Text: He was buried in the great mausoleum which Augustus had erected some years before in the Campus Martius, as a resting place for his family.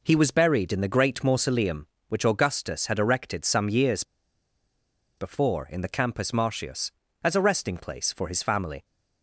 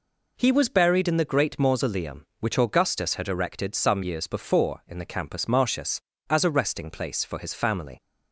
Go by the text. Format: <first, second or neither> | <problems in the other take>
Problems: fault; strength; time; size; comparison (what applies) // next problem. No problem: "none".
second | pauses between "years" and "before"; at 4.0 s; 1.1 s long